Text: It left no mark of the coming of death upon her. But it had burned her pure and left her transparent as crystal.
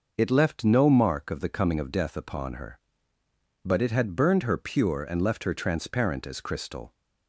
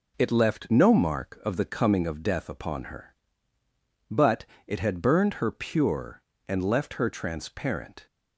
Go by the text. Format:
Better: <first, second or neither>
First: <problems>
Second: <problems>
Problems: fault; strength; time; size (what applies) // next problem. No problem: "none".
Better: first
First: none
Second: pauses between "But" and "it"; slight; at 4.4 s; 0.22 s long // stops before "as crystal"; at 8.0 s